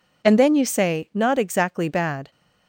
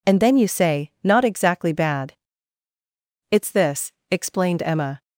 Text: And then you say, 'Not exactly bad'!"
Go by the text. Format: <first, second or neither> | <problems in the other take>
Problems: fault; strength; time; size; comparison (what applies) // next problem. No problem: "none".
first | goes on to say "It's this explained Emma"; strong; from 3.2 s on; 1.7 s long